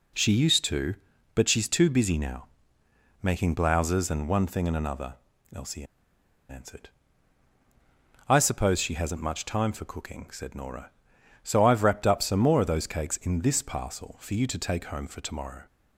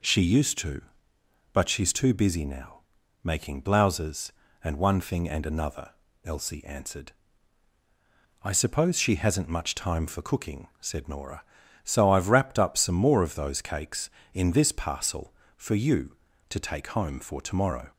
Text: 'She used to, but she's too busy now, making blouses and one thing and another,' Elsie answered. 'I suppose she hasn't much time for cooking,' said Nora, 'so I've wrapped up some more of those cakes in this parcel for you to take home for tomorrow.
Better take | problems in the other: second | pauses between "Elsie" and "answered"; noticeable; at 5.8 s; 0.65 s long

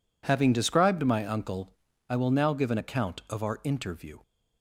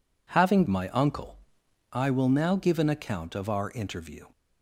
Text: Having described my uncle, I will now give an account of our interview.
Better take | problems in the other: first | skips "described"; at 0.6 s

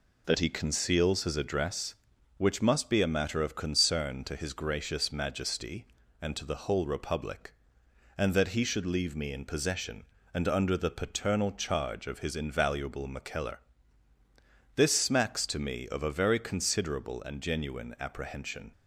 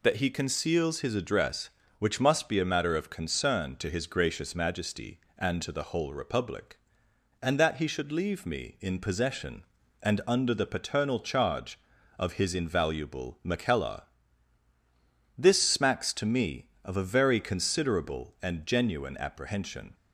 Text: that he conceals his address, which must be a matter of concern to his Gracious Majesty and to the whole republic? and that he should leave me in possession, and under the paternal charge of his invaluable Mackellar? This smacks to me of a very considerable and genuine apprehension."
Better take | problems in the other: neither | none

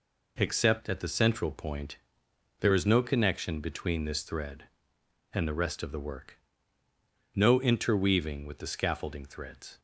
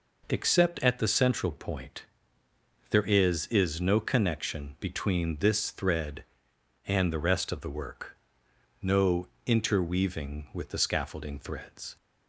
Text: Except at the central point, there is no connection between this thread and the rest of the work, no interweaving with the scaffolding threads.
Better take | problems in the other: first | says "is" twice; at 3.4 s // pauses between "no" and "interweaving"; slight; at 9.2 s; 0.16 s long

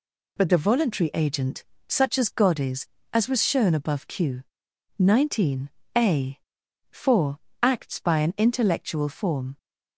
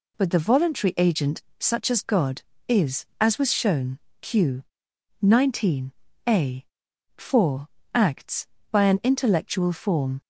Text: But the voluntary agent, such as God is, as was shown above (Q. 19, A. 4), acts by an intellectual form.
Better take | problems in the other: first | skips "above"; at 4.0 s

